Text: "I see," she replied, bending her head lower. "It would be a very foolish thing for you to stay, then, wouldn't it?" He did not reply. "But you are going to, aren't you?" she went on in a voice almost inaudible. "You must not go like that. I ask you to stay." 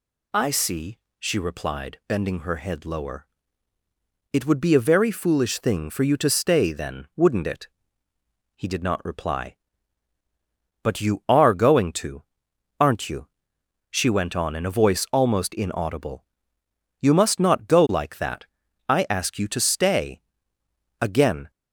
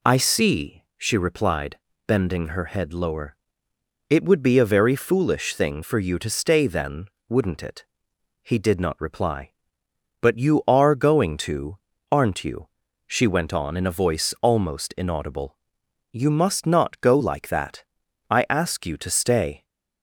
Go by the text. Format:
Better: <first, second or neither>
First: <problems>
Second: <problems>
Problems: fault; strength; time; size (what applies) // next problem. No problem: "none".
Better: second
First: goes on to say "Again"; from 21.0 s on; 0.50 s long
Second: none